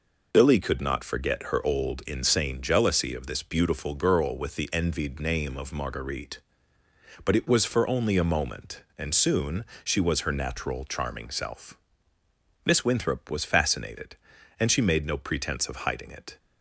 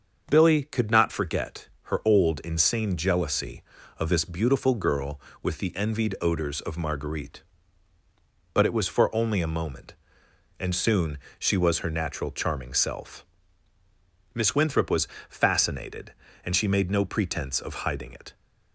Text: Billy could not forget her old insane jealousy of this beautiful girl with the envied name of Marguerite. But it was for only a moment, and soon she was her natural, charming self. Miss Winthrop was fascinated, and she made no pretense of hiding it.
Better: first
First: pauses between "soon" and "she"; slight; at 9.6 s; 0.18 s long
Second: starts louder than the rest; until 1.2 s; 6.5 dB // pauses between "forget" and "her"; slight; at 1.6 s; 0.16 s long // says "odors" for "name"; at 6.1 s // pauses between "soon" and "she"; slight; at 11.1 s; 0.18 s long // pauses between "was" and "fascinated"; slight; at 15.0 s; 0.22 s long

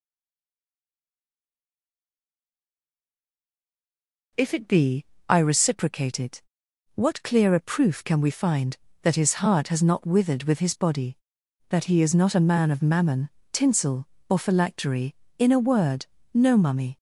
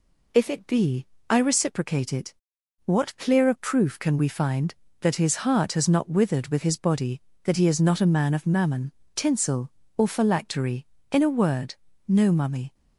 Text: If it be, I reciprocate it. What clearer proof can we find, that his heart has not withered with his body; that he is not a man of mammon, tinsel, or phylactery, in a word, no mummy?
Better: second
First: stays silent before the first word; strong; until 4.3 s; 4.3 s long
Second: none

